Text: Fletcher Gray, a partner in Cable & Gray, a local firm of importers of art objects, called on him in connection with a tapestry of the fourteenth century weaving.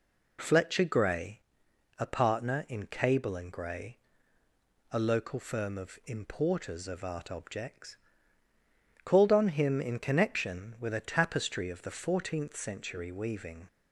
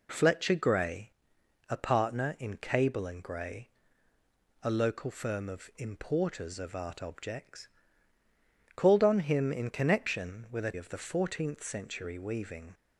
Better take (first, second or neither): first